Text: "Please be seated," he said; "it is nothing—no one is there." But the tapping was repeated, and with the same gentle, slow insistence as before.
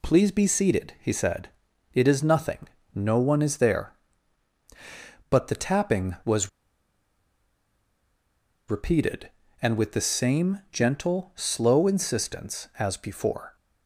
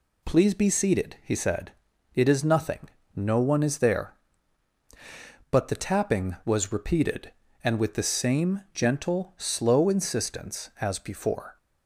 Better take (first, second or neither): second